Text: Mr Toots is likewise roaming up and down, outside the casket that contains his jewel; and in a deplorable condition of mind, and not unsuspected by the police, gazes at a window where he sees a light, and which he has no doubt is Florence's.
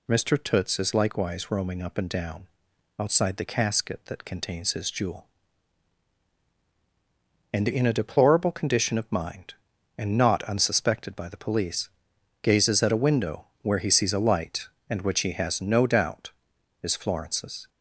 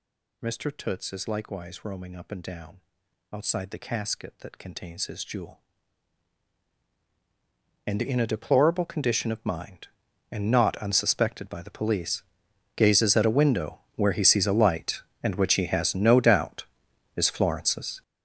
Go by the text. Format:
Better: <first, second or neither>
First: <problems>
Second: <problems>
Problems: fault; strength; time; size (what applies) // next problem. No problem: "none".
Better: first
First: pauses between "window" and "where"; slight; at 13.4 s; 0.16 s long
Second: gets louder; strong; throughout; 13 dB // pauses between "window" and "where"; slight; at 13.7 s; 0.16 s long